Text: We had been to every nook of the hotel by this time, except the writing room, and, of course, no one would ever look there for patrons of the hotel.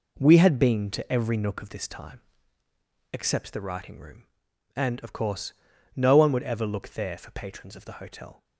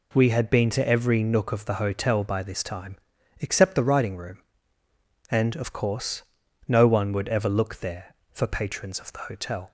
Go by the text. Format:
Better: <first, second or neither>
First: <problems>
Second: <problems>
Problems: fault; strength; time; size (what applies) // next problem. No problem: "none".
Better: second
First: skips "the hotel by"; at 1.6 s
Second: none